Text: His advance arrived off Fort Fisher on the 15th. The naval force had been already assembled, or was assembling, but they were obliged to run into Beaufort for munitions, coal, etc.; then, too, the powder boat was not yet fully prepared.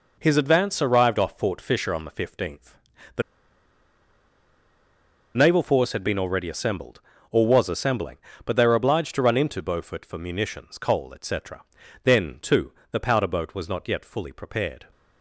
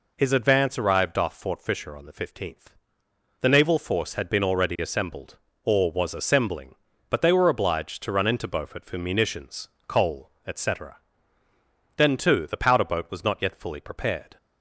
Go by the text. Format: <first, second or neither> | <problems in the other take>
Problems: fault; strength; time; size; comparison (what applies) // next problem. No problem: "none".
second | pauses between "The" and "naval"; strong; at 3.2 s; 2.1 s long